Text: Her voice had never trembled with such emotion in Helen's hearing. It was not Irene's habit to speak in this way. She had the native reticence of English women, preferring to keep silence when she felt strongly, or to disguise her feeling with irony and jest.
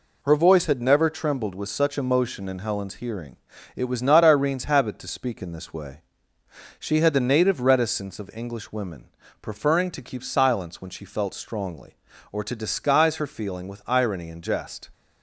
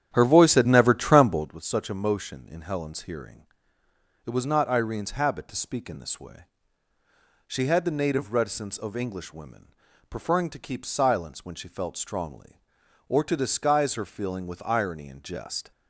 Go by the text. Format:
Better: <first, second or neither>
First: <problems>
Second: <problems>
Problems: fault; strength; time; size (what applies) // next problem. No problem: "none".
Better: first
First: none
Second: starts louder than the rest; strong; until 1.5 s; 9.5 dB